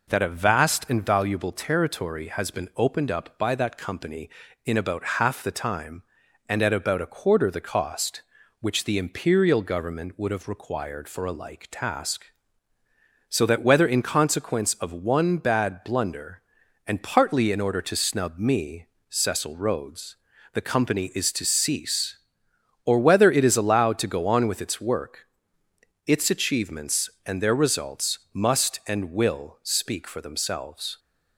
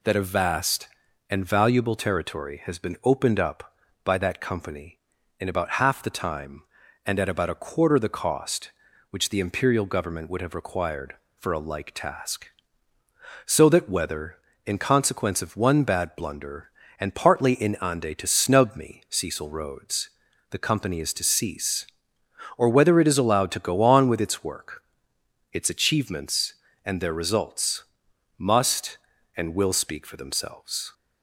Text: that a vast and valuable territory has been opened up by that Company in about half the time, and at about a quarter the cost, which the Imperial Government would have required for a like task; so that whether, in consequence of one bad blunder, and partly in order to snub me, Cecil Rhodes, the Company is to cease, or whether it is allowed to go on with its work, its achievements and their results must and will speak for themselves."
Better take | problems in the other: first | says "ande" for "order"; at 17.7 s // pauses between "results" and "must"; noticeable; at 27.8 s; 0.56 s long; slight in the first

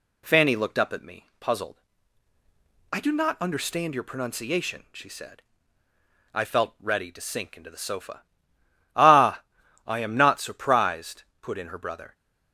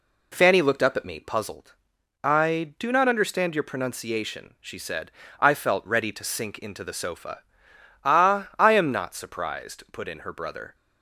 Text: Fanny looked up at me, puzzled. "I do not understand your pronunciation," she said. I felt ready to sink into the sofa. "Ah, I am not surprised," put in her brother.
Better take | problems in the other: neither | none

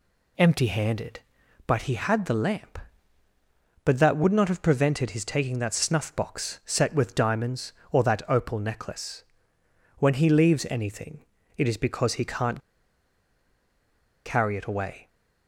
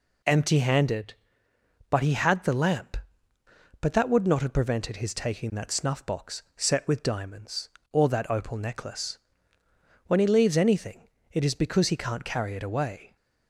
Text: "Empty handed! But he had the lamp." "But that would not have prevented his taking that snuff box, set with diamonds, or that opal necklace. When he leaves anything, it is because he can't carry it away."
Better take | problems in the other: second | pauses between "can't" and "carry"; strong; at 12.5 s; 1.6 s long

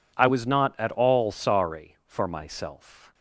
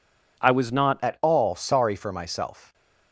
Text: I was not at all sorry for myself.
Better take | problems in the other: first | changes voice at "at"; from 1.0 s on; 1.7 s long

